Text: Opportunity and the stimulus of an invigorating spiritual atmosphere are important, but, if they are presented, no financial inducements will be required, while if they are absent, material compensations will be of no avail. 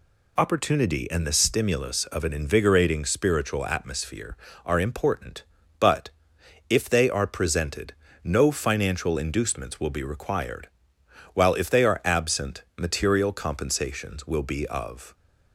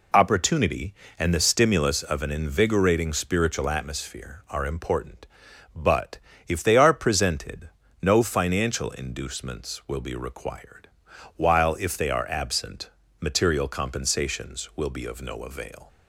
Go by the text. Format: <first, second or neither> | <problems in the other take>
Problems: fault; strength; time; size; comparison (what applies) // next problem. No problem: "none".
second | stops before "no avail"; at 15.1 s